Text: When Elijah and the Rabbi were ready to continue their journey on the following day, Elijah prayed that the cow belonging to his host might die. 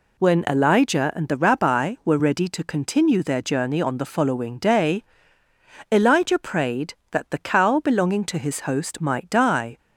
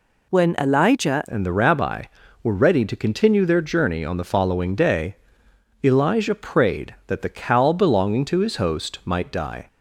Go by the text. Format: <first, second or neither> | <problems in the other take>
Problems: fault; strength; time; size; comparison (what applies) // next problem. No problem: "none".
first | changes voice at "and"; from 1.2 s on; 8.4 s long